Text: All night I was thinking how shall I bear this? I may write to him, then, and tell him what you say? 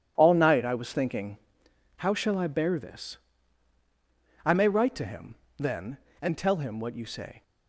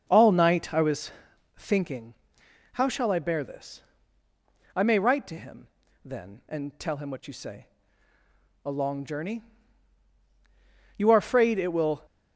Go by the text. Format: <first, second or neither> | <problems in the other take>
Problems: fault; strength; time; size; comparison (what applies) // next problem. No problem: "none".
first | starts louder than the rest; until 1.0 s; 6 dB // pauses between "was" and "thinking"; noticeable; at 1.1 s; 0.46 s long // pauses between "thinking" and "how"; noticeable; at 2.1 s; 0.60 s long; noticeable in the first // goes on to say "A long journey You are afraid it will"; strong; from 8.6 s on; 3.4 s long